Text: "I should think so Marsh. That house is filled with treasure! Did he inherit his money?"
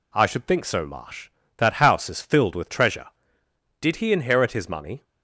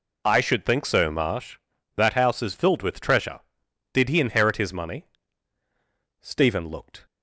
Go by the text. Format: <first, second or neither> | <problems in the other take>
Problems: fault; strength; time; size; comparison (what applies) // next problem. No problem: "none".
first | goes on to say "Stephen looked"; noticeable; from 6.1 s on; 0.86 s long